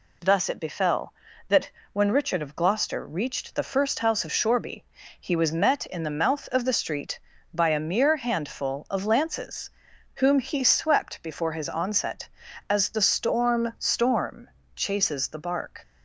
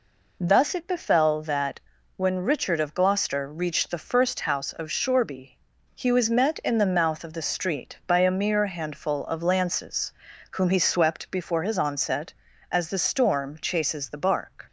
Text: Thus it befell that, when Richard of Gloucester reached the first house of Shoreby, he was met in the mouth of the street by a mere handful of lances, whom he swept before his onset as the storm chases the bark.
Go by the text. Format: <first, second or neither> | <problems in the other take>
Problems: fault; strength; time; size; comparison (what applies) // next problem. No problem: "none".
second | says "storm" twice; at 13.7 s